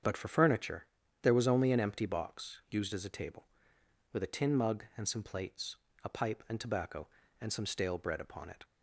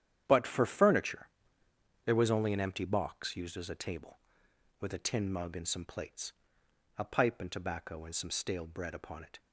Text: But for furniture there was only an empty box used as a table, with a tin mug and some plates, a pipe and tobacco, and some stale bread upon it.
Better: first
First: starts louder than the rest; strong; until 1.4 s; 7.5 dB // pauses between "furniture" and "there"; at 0.8 s; 0.38 s long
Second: gets quieter; strong; throughout; 11.5 dB // starts louder than the rest; strong; until 1.2 s; 10 dB // pauses between "furniture" and "there"; noticeable; at 1.2 s; 0.78 s long

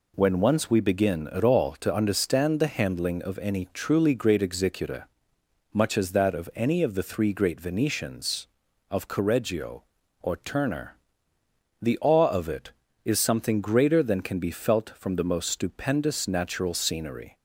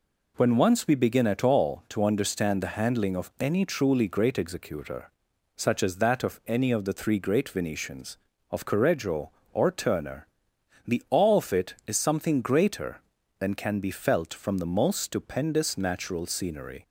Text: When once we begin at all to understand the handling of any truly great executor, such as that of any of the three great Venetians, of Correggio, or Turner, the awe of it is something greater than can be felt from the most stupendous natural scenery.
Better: second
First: says "much" for "such"; at 5.7 s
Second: none

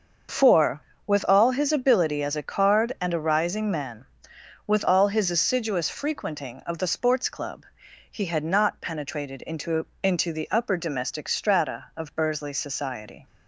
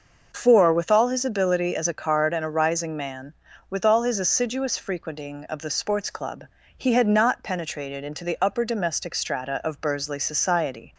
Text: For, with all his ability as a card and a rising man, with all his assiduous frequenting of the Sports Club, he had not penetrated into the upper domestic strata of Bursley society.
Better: second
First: starts louder than the rest; until 1.6 s; 6.5 dB // says "into" twice; at 10.0 s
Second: none

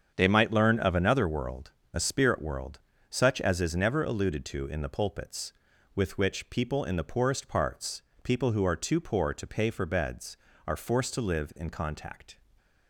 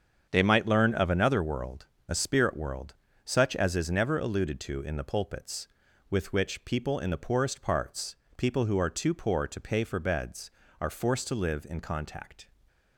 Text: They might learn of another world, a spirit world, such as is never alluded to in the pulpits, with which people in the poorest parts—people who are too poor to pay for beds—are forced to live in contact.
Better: neither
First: starts louder than the rest; strong; until 1.1 s; 7.5 dB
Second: starts louder than the rest; strong; until 1.3 s; 7.5 dB

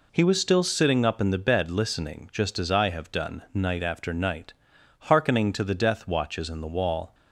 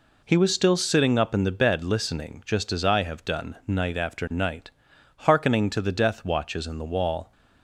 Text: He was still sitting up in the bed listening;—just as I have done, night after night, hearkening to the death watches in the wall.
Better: neither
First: none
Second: none

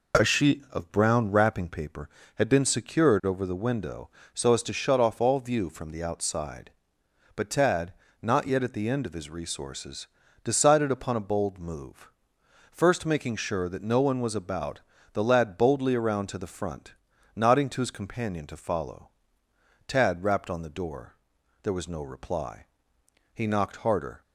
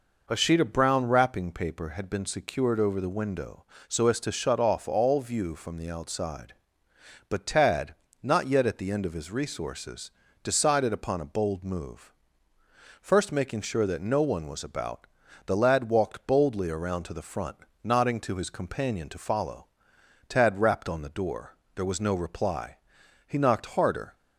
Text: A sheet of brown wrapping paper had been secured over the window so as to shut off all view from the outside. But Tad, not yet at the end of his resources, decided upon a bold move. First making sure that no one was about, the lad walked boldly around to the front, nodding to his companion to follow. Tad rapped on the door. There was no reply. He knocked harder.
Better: second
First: skips "walked"; at 15.5 s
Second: none

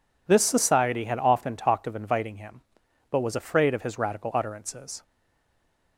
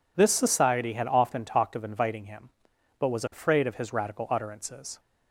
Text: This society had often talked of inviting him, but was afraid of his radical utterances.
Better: second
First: stays silent after the last word; slight; from 5.0 s on; 0.9 s long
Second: none

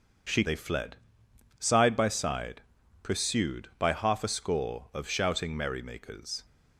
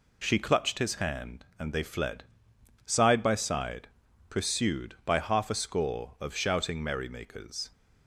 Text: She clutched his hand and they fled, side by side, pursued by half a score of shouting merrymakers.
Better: second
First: skips "clutched his hand and"; at 0.4 s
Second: none

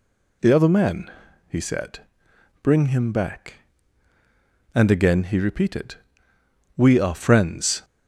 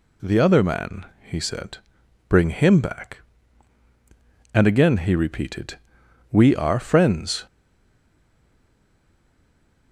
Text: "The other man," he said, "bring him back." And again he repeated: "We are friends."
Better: first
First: none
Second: stays silent after the last word; from 7.4 s on; 2.5 s long

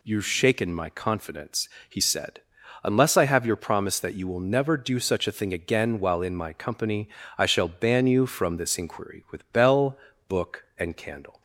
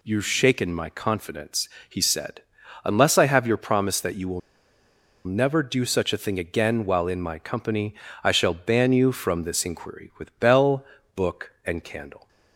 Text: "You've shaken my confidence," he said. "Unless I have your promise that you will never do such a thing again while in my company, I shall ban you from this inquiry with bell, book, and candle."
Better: first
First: none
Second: pauses between "will" and "never"; noticeable; at 4.4 s; 0.85 s long

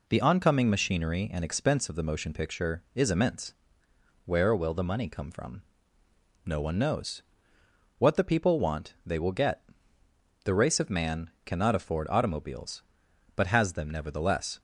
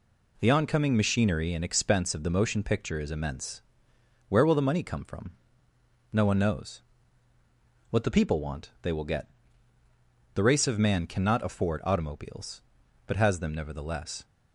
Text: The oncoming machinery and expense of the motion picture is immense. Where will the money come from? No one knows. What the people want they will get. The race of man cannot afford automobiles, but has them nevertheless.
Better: neither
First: none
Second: none

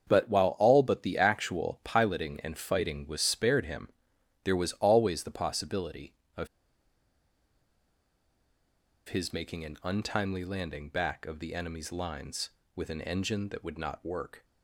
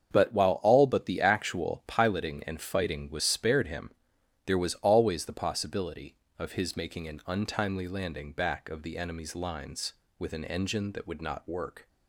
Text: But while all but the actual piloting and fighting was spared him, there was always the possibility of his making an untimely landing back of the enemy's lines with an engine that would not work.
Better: second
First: starts louder than the rest; strong; until 1.1 s; 7 dB // pauses between "of" and "his"; strong; at 6.4 s; 2.6 s long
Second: starts louder than the rest; strong; until 1.1 s; 7 dB

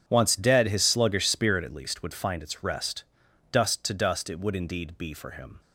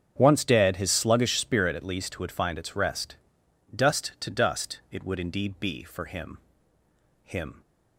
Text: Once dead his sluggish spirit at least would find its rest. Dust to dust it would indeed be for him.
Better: first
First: starts louder than the rest; strong; until 1.0 s; 8 dB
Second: starts louder than the rest; strong; until 1.2 s; 7.5 dB // says "him" twice; at 7.2 s

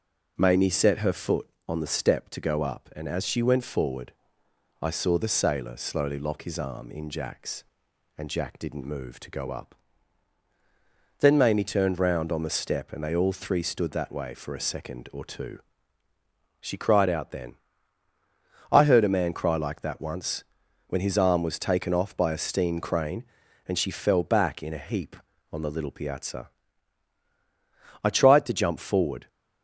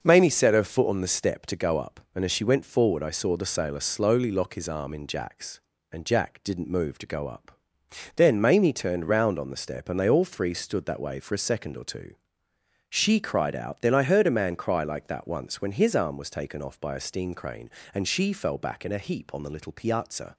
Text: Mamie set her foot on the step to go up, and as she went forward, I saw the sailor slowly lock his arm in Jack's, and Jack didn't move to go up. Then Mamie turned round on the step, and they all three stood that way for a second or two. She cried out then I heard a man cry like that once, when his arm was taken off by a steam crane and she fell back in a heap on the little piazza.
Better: second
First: pauses between "then" and "I"; at 17.5 s; 1.1 s long // goes on to say "I tried to jump forward"; noticeable; from 28.0 s on; 1.2 s long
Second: none

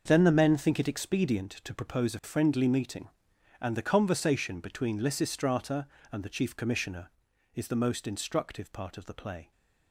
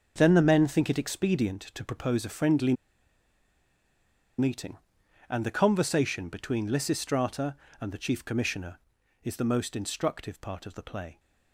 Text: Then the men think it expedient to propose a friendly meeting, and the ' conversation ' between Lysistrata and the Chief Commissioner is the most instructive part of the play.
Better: first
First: starts louder than the rest; until 1.0 s; 6.5 dB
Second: starts louder than the rest; until 1.1 s; 6.5 dB // pauses between "friendly" and "meeting"; strong; at 2.7 s; 1.6 s long

